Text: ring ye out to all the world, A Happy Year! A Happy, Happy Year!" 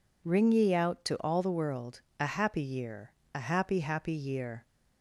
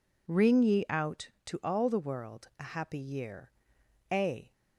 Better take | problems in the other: first | stops before "Happy Happy Year"; at 4.5 s

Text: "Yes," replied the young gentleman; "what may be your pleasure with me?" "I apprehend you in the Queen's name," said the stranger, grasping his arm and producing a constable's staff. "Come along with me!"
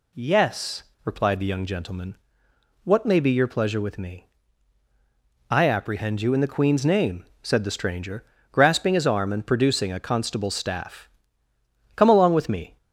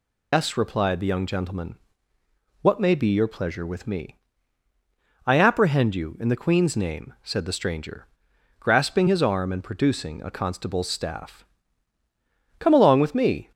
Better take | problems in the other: first | loses the start of "Yes"; at 0.3 s; 145 ms

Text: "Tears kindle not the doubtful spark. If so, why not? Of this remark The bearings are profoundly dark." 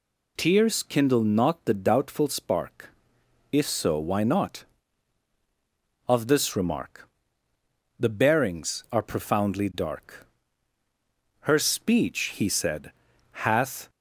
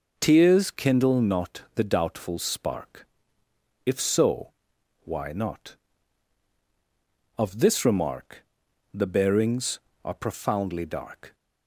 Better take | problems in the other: second | pauses between "remark" and "The"; noticeable; at 7.0 s; 0.90 s long; noticeable in the second // goes on to say "Her speech he said hath"; strong; from 11.4 s on; 2.4 s long

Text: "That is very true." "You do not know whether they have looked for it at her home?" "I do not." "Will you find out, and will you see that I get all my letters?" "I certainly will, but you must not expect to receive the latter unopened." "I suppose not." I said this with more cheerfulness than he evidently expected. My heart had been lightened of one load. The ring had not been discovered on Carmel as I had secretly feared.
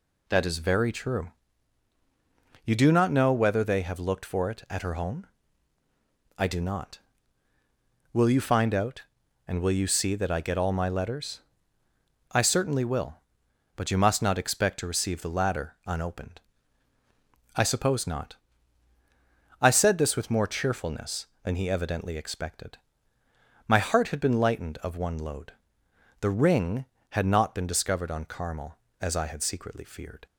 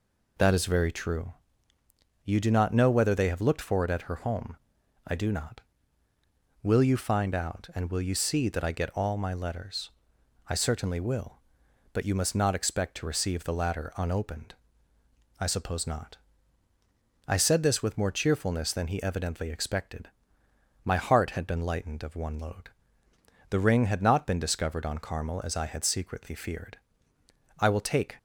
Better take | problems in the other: first | goes on to say "I will take"; from 27.5 s on; 0.58 s long

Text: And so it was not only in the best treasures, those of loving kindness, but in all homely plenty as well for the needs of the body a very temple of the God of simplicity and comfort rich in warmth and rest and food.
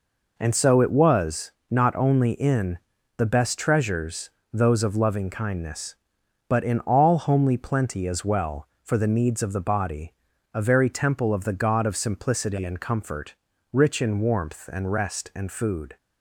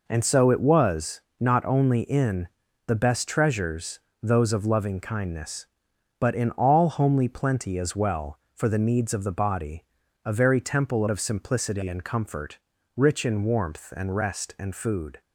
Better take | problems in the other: first | pauses between "was" and "not"; slight; at 1.1 s; 0.20 s long; slight in the first // pauses between "in" and "the"; at 2.4 s; 0.38 s long; also in the first // pauses between "body" and "a"; at 9.8 s; 0.40 s long; also in the first // skips "of the God"; at 11.0 s // pauses between "comfort" and "rich"; at 12.5 s; 0.38 s long; also in the first

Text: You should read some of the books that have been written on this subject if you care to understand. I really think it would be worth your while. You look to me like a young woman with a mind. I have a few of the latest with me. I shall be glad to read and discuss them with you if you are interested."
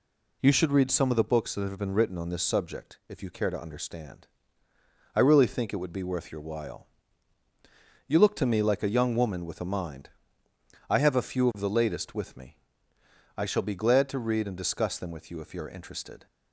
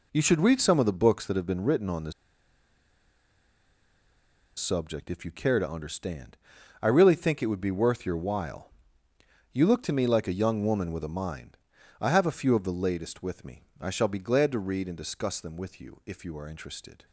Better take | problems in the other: first | pauses between "this" and "subject"; strong; at 2.1 s; 2.4 s long

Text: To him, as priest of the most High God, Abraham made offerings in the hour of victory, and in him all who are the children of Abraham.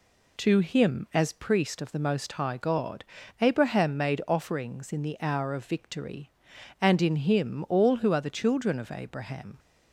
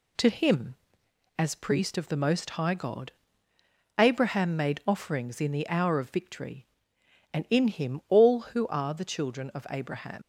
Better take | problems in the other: first | leaves "Abraham" unfinished; at 10.2 s; 115 ms

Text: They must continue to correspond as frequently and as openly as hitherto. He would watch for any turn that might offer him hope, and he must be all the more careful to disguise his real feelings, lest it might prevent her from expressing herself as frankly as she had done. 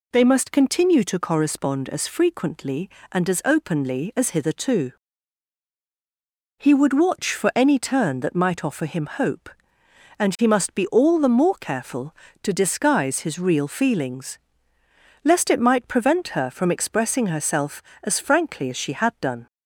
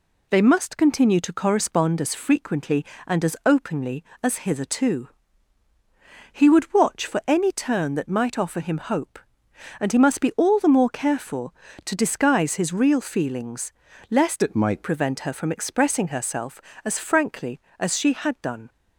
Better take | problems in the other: first | changes voice from "it" to "might"; from 14.4 to 14.8 s; 0.4 s long

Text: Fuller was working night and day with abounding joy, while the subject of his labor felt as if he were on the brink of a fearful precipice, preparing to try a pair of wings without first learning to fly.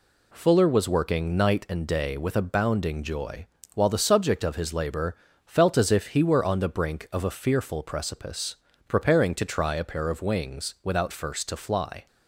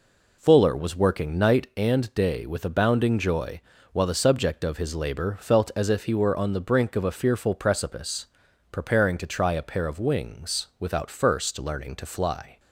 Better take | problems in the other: second | pauses between "labor" and "felt"; slight; at 5.1 s; 0.30 s long // skips "learning"; at 11.4 s

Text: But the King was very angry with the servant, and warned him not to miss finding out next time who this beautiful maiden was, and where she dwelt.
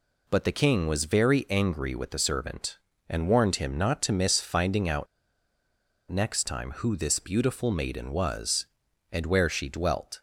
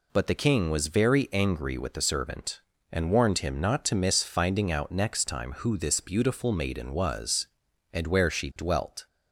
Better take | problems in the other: second | pauses between "out" and "next"; at 5.0 s; 1.0 s long

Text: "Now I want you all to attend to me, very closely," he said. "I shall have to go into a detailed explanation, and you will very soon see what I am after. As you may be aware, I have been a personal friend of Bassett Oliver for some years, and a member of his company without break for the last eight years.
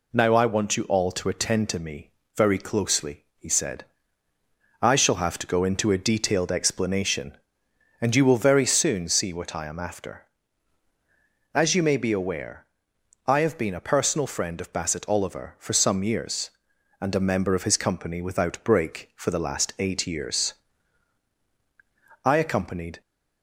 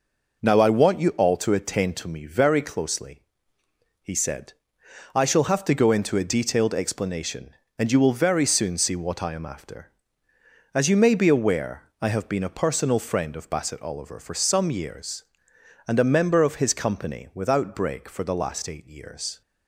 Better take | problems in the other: second | goes on to say "I accompanied"; noticeable; from 22.2 s on; 0.76 s long

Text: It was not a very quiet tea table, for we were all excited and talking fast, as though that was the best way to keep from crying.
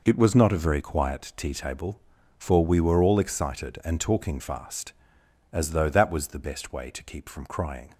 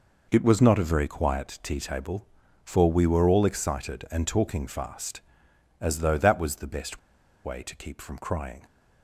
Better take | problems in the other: first | pauses between "best" and "way"; at 6.9 s; 0.45 s long

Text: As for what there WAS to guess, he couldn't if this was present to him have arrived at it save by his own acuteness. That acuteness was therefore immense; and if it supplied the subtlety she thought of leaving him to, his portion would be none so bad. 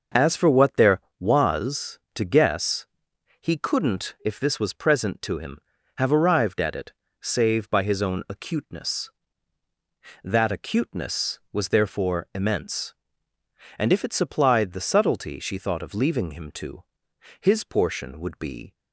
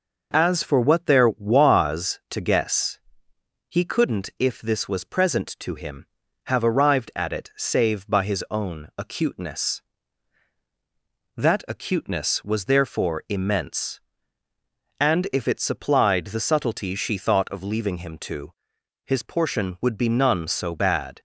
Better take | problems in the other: second | starts louder than the rest; noticeable; until 1.3 s; 6 dB // pauses between "it" and "save"; slight; at 6.9 s; 0.28 s long // stops before "none so bad"; at 18.7 s

